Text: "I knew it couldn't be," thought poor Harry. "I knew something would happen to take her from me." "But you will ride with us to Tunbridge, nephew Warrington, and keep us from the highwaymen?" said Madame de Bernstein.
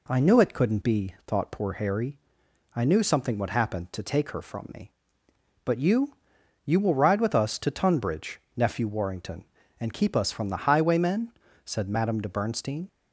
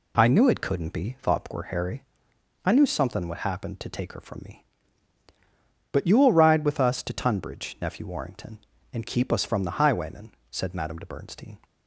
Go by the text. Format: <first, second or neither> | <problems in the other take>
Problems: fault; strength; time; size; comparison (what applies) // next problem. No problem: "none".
second | says "you" twice; at 6.6 s